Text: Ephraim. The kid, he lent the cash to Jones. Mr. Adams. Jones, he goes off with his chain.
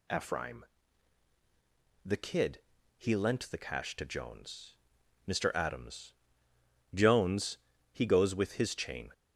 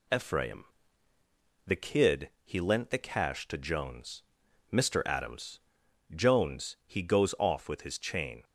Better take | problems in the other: second | skips "off"; at 8.3 s

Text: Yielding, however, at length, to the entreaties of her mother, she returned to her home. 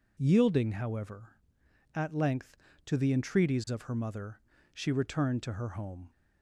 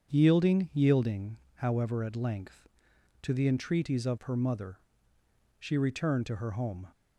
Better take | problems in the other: first | starts louder than the rest; strong; until 1.1 s; 7 dB // says "Yielding" twice; at 0.7 s

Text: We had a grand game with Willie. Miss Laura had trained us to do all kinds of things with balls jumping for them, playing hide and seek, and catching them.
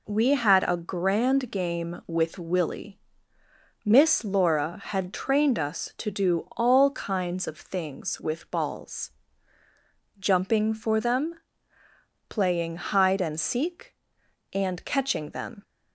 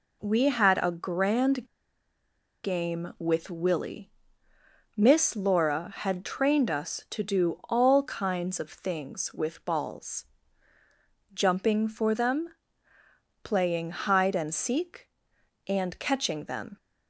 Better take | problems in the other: first | pauses between "grand" and "game"; at 1.6 s; 0.98 s long // pauses between "balls" and "jumping"; at 10.2 s; 1.1 s long; also in the first

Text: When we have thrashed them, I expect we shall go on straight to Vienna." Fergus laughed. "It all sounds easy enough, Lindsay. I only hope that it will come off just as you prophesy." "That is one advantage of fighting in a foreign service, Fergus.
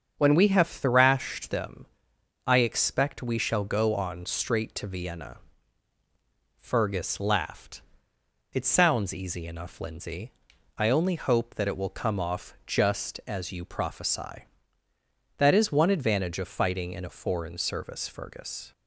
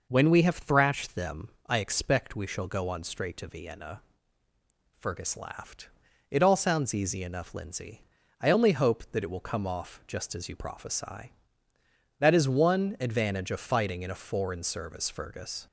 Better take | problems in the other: second | starts louder than the rest; strong; until 1.1 s; 7.5 dB // skips "all"; at 8.6 s

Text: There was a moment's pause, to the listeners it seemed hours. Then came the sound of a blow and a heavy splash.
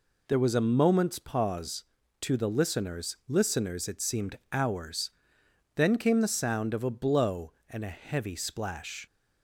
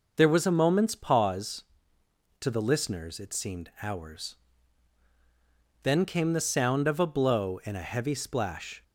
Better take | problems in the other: second | says "listeners" twice; at 3.2 s // pauses between "seemed" and "hours"; slight; at 4.3 s; 0.16 s long

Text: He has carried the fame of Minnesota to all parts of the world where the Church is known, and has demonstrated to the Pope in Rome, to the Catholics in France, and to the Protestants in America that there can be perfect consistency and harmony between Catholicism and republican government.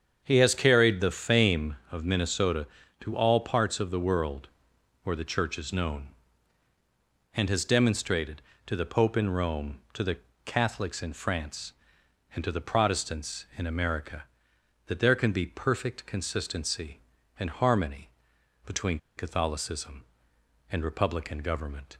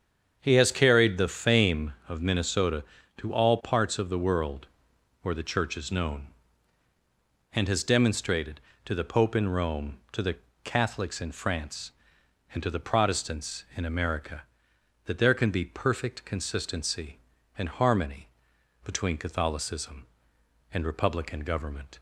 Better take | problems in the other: second | starts louder than the rest; strong; until 1.2 s; 7.5 dB; strong in the second // pauses between "world" and "where"; noticeable; at 4.4 s; 0.56 s long; noticeable in the second // pauses between "the" and "Catholics"; slight; at 10.1 s; 0.30 s long; slight in the second // pauses between "harmony" and "between"; noticeable; at 18.0 s; 0.56 s long; noticeable in the second // pauses between "between" and "Catholicism"; slight; at 18.9 s; 0.19 s long

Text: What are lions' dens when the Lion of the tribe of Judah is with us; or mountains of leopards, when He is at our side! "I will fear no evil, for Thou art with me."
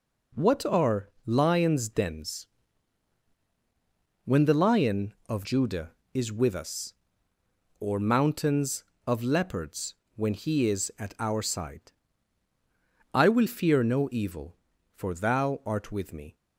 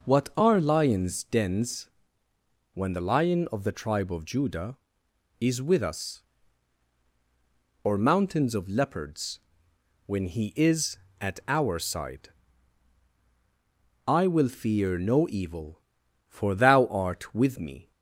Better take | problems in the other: second | pauses between "are" and "lions"; slight; at 1.0 s; 0.18 s long // pauses between "dens" and "when"; strong; at 2.4 s; 1.7 s long; noticeable in the second // skips "the tribe of"; at 5.4 s

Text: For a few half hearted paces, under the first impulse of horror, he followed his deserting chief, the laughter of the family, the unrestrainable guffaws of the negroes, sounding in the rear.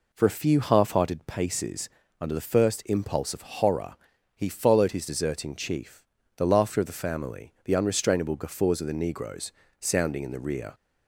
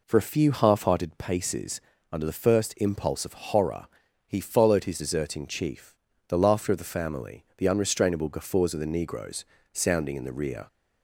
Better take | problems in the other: neither | none

